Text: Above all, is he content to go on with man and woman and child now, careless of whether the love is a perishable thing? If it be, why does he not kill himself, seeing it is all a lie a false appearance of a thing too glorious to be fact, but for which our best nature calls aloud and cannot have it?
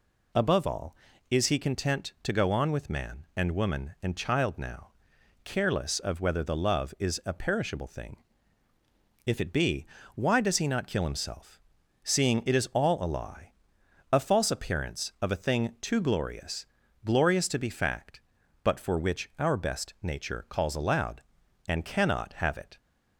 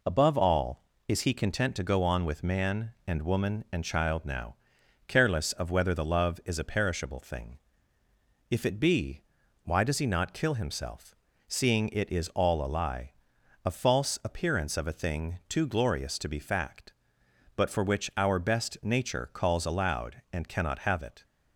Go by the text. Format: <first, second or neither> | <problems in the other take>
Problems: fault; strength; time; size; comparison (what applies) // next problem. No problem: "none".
second | pauses between "lie" and "a"; noticeable; at 13.5 s; 0.58 s long; noticeable in the second // says "glorious" twice; at 17.0 s